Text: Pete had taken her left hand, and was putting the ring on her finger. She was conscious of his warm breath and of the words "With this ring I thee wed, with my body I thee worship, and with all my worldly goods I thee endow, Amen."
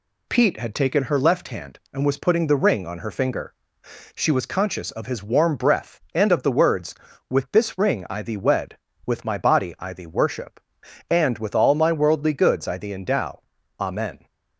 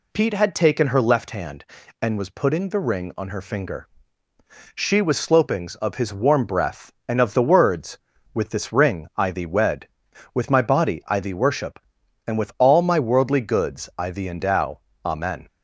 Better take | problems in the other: first | says "slopings" for "conscious"; at 5.1 s

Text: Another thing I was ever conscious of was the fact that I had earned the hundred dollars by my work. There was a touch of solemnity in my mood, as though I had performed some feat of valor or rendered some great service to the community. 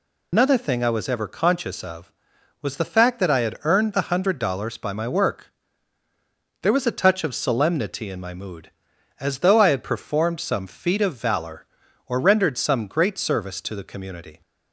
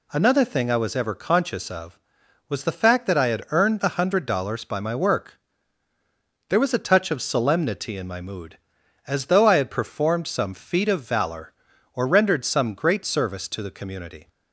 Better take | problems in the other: second | loses the start of "Another"; at 0.3 s; 105 ms

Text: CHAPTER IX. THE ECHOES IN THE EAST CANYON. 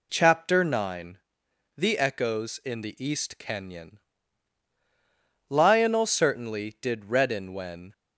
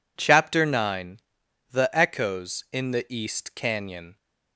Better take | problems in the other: second | goes on to say "LIONEL certainly did redden when"; strong; from 5.4 s on; 2.4 s long

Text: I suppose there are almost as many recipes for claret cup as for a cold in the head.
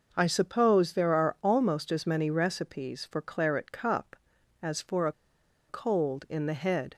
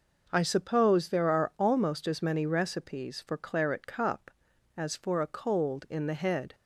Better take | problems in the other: second | pauses between "a" and "cold"; noticeable; at 5.1 s; 0.56 s long

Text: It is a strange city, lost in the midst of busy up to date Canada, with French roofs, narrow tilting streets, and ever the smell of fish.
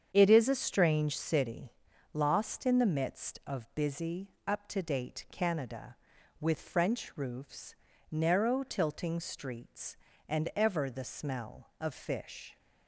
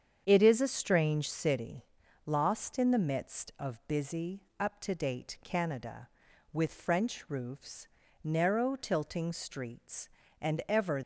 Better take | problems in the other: first | starts louder than the rest; strong; until 1.2 s; 8 dB; strong in the first // pauses between "busy" and "up"; slight; at 4.4 s; 0.16 s long; slight in the first // stops before "the smell of fish"; at 11.0 s

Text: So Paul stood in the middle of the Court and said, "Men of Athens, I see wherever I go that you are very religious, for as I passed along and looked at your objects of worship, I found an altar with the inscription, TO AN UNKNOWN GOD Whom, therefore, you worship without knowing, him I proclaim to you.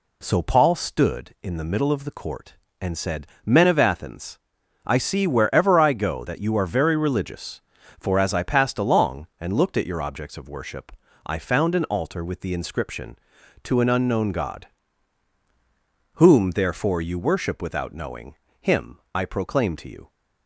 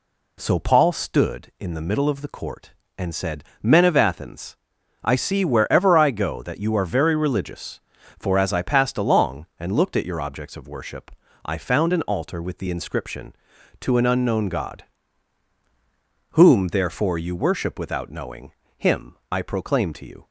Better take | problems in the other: neither | pauses between "GOD" and "Whom"; strong; the same in both // pauses between "him" and "I"; slight; the same in both

